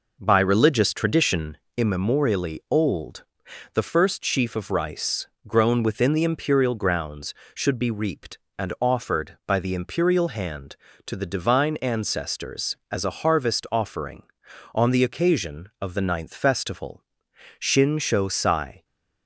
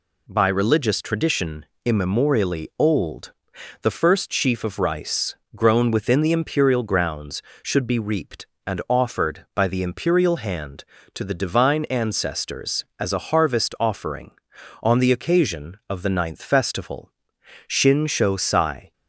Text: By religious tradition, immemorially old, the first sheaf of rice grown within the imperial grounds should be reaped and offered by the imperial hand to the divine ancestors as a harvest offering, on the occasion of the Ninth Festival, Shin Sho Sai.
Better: second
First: starts louder than the rest; noticeable; until 1.7 s; 5 dB // pauses between "rice" and "grown"; slight; at 5.2 s; 0.18 s long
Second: pauses between "rice" and "grown"; slight; at 5.3 s; 0.18 s long

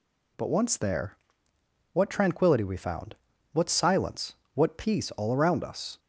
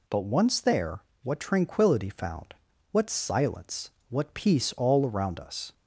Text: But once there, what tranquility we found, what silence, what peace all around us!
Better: first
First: none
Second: skips "we"; at 2.0 s

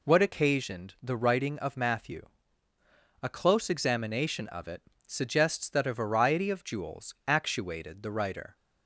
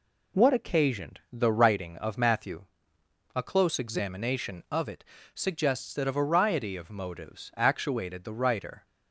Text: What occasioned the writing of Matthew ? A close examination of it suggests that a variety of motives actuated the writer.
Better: second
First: pauses between "it" and "suggests"; slight; at 4.8 s; 0.24 s long // says "jewels" for "motives"; at 6.6 s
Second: pauses between "it" and "suggests"; slight; at 5.0 s; 0.28 s long

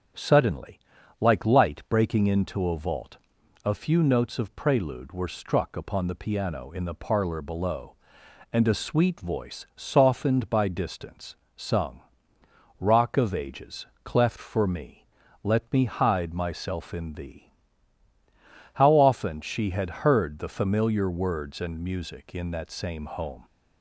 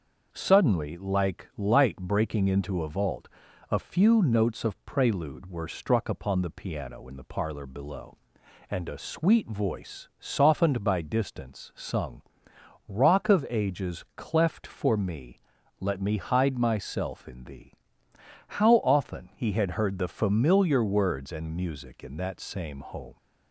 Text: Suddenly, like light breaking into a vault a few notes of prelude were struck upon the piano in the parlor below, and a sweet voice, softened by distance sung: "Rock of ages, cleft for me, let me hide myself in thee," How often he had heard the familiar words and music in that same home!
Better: second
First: starts louder than the rest; until 1.5 s; 7 dB // pauses between "vault" and "a"; noticeable; at 3.1 s; 0.48 s long // pauses between "distance" and "sung"; slight; at 11.3 s; 0.20 s long // says "she" for "he"; at 19.4 s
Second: starts louder than the rest; until 1.3 s; 6.5 dB // pauses between "vault" and "a"; at 3.2 s; 0.42 s long

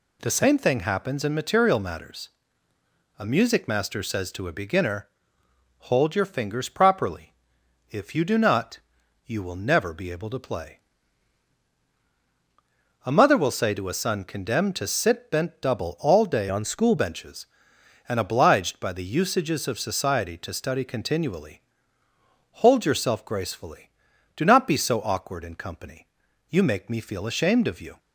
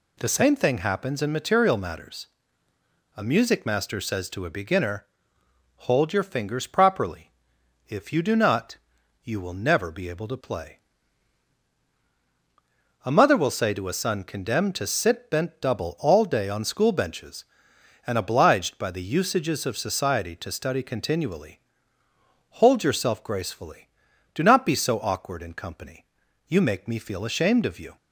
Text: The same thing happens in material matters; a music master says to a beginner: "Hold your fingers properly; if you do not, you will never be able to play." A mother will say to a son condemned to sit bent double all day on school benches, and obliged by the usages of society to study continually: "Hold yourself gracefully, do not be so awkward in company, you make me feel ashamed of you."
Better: second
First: changes voice from "on" to "school"; from 16.4 to 16.9 s; 0.5 s long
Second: none

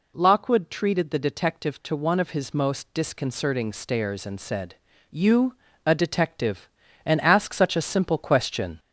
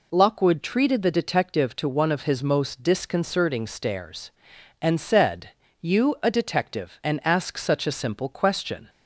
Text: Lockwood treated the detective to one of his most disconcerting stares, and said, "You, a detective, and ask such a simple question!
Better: second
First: gets louder; slight; throughout; 3 dB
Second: none

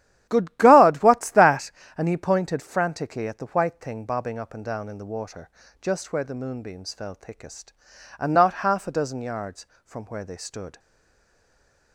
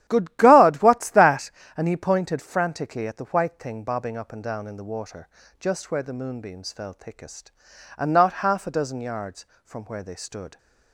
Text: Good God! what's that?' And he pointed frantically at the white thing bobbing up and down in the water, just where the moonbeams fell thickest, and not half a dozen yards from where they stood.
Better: second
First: starts louder than the rest; strong; until 1.3 s; 11.5 dB // stays silent after the last word; noticeable; from 10.7 s on; 1.2 s long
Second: starts louder than the rest; strong; until 1.0 s; 11.5 dB

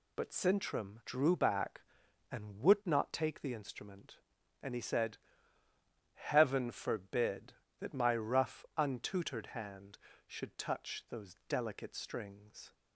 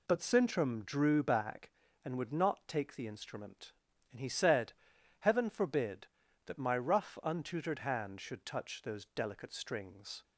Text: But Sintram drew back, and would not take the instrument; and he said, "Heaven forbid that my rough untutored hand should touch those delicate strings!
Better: neither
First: none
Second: none

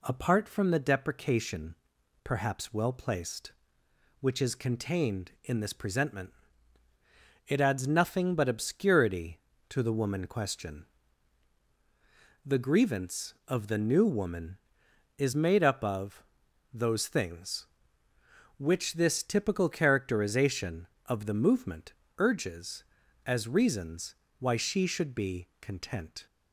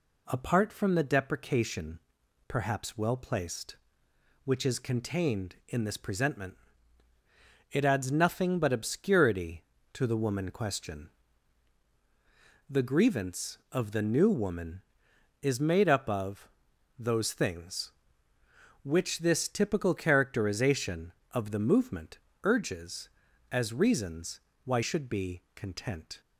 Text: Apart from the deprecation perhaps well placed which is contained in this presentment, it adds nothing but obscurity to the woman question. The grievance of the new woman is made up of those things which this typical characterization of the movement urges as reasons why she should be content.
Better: first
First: pauses between "deprecation" and "perhaps"; noticeable; at 1.7 s; 0.48 s long // pauses between "of" and "those"; noticeable; at 16.2 s; 0.48 s long // pauses between "movement" and "urges"; slight; at 21.9 s; 0.26 s long // pauses between "reasons" and "why"; slight; at 24.1 s; 0.24 s long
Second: pauses between "deprecation" and "perhaps"; noticeable; at 1.9 s; 0.48 s long // pauses between "of" and "those"; noticeable; at 16.4 s; 0.48 s long // pauses between "movement" and "urges"; slight; at 22.1 s; 0.26 s long // pauses between "reasons" and "why"; slight; at 24.3 s; 0.24 s long // skips "she"; at 24.8 s

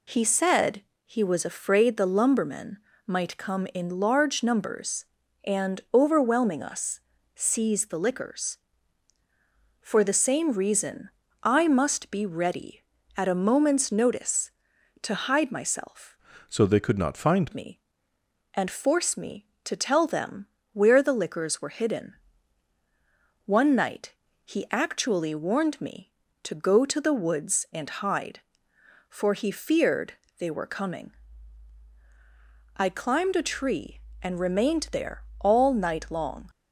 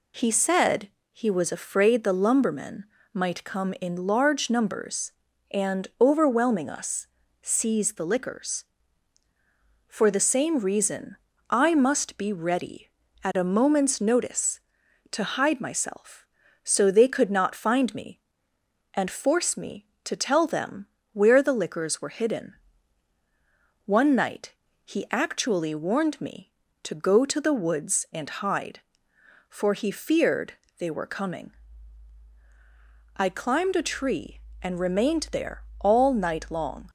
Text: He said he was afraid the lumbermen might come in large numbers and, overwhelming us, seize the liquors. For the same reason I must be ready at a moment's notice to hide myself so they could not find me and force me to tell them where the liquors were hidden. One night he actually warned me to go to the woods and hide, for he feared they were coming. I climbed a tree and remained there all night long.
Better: second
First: pauses between "said" and "he"; slight; at 0.8 s; 0.24 s long // pauses between "lumbermen" and "might"; slight; at 2.7 s; 0.28 s long // pauses between "reason" and "I"; slight; at 11.1 s; 0.32 s long // changes voice from "so" to "find"; from 16.4 to 17.5 s; 1.1 s long // pauses between "them" and "where"; slight; at 20.4 s; 0.26 s long // pauses between "night" and "he"; slight; at 24.1 s; 0.30 s long // pauses between "feared" and "they"; slight; at 30.1 s; 0.26 s long // pauses between "there" and "all"; slight; at 35.2 s; 0.18 s long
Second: pauses between "said" and "he"; slight; at 0.8 s; 0.24 s long // pauses between "lumbermen" and "might"; slight; at 2.8 s; 0.28 s long // pauses between "reason" and "I"; slight; at 11.1 s; 0.32 s long // pauses between "them" and "where"; slight; at 20.8 s; 0.26 s long // pauses between "night" and "he"; slight; at 24.5 s; 0.30 s long // pauses between "feared" and "they"; slight; at 30.5 s; 0.26 s long // pauses between "there" and "all"; slight; at 35.6 s; 0.18 s long

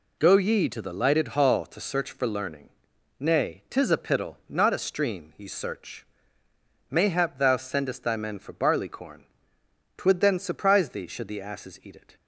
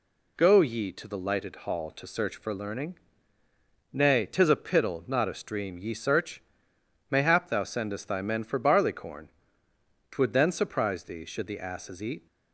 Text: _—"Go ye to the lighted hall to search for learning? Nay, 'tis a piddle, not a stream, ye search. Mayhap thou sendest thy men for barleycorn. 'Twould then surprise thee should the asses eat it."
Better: first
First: none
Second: stops before "it"; at 12.2 s

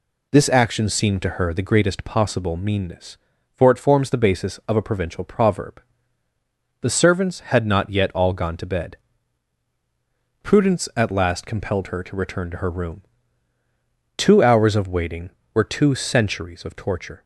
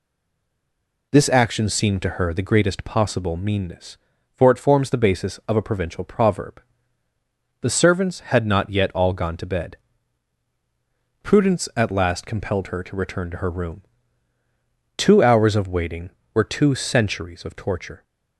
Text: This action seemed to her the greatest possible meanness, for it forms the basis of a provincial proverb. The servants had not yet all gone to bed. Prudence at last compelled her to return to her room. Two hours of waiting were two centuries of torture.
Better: first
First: none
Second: stays silent before the first word; until 1.1 s; 1.1 s long

